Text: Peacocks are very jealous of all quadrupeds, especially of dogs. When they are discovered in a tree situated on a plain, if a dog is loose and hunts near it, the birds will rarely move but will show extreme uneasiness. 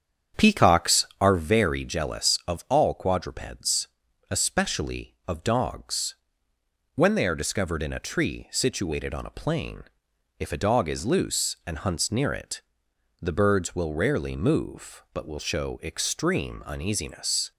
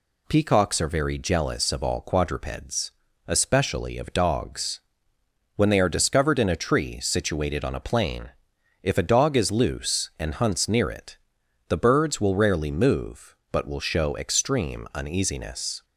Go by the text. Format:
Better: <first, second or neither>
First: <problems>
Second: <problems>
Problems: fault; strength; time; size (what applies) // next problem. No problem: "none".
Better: second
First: starts louder than the rest; strong; until 1.5 s; 8 dB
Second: none